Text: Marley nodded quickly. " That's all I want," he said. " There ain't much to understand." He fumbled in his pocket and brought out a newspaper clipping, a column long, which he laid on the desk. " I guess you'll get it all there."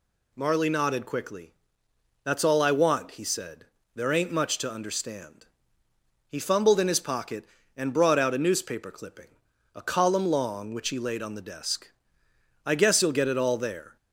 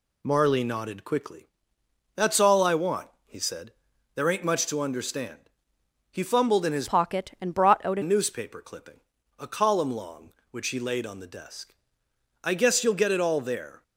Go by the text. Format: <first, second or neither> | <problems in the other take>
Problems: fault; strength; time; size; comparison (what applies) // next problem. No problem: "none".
first | changes voice from "pocket" to "a"; from 6.8 to 8.0 s; 1.2 s long